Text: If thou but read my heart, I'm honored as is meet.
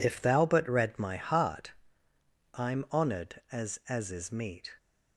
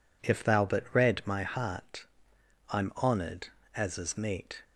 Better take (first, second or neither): second